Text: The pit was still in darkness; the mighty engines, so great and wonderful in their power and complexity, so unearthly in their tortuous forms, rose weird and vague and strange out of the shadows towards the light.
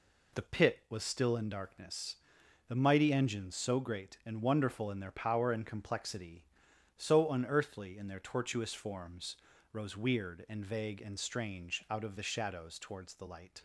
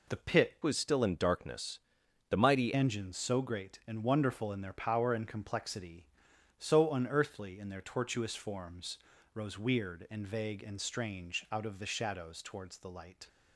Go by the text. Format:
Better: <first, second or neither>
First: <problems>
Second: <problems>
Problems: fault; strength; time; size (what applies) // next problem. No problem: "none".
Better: first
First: none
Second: changes voice from "was" to "mighty"; from 0.6 to 2.7 s; 2.1 s long